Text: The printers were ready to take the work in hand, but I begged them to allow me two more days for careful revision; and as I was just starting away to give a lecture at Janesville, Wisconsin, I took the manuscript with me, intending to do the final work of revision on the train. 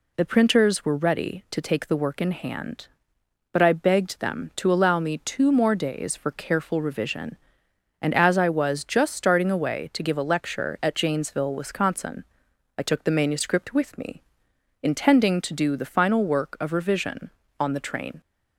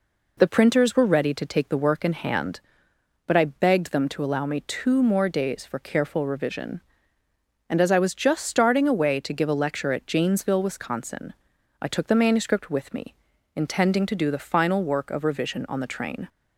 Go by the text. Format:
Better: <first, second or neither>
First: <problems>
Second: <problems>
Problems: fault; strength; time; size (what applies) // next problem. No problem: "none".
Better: neither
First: none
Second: none